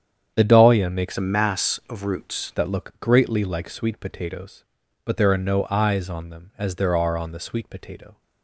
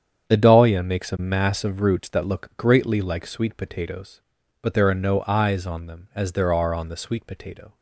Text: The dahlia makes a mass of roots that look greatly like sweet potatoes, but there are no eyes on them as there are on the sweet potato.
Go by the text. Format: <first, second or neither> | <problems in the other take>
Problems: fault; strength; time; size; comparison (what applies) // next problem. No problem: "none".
second | starts louder than the rest; strong; until 1.3 s; 8.5 dB; strong in the second // changes voice from "a" to "roots"; from 1.1 to 2.5 s; 1.4 s long